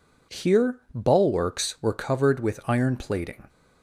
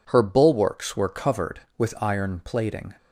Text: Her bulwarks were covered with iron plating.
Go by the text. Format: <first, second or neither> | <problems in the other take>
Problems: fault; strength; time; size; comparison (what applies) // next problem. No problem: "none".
second | says "Here" for "Her"; at 0.3 s